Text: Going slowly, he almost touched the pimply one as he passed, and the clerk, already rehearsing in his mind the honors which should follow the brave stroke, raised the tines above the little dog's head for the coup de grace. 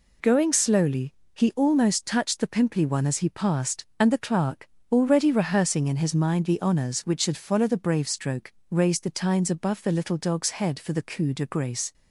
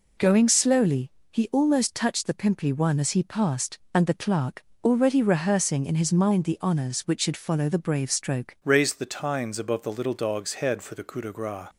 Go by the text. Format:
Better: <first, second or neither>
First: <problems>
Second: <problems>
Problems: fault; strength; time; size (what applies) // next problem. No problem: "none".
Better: first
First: none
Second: changes voice at "raised"; from 8.6 s on; 3.0 s long